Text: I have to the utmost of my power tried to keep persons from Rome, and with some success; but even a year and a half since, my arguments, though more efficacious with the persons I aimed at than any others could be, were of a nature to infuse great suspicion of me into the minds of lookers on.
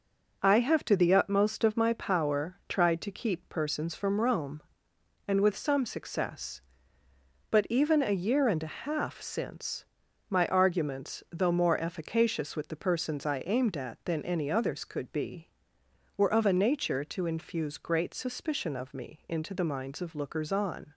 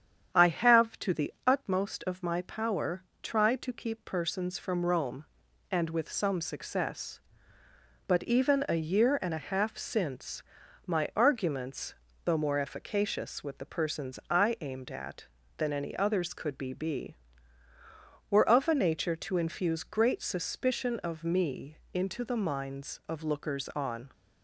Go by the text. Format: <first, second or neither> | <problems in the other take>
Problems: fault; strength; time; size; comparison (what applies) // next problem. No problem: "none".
first | starts louder than the rest; strong; until 1.4 s; 8.5 dB // pauses between "power" and "tried"; slight; at 3.0 s; 0.20 s long // says "be" twice; at 16.7 s // pauses between "me" and "into"; slight; at 21.7 s; 0.18 s long